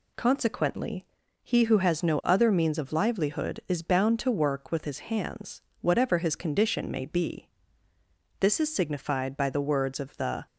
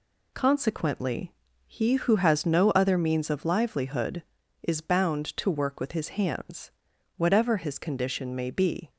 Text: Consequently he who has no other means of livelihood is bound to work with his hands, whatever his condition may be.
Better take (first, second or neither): second